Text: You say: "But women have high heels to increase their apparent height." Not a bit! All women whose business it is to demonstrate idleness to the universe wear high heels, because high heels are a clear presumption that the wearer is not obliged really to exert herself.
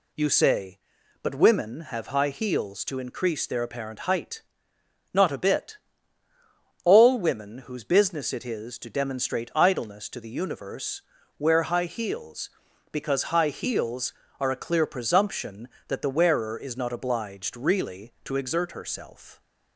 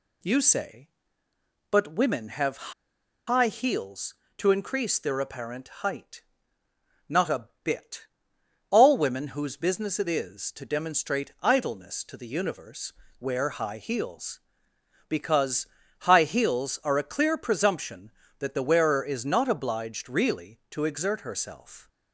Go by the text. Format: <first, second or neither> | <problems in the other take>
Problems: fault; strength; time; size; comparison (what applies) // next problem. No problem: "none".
first | pauses between "have" and "high"; noticeable; at 2.7 s; 0.55 s long // pauses between "a" and "bit"; slight; at 7.4 s; 0.16 s long // pauses between "universe" and "wear"; slight; at 12.9 s; 0.28 s long; also in the first // pauses between "because" and "high"; slight; at 15.6 s; 0.34 s long